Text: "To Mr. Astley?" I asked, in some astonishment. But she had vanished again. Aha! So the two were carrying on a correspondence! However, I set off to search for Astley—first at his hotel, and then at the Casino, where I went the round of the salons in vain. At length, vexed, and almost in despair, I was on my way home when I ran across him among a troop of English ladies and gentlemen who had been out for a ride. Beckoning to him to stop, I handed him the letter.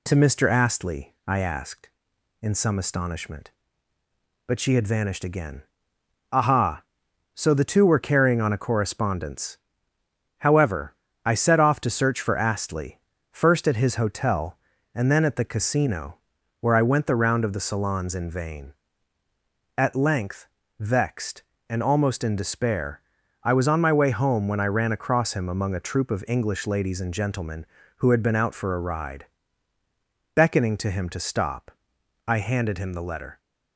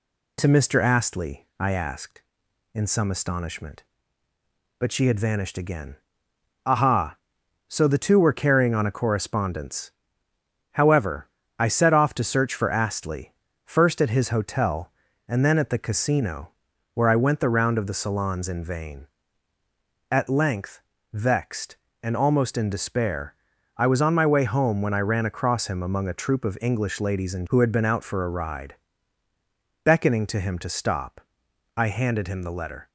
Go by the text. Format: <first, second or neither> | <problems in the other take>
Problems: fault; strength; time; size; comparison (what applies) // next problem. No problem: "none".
first | skips "gentlemen"; at 27.4 s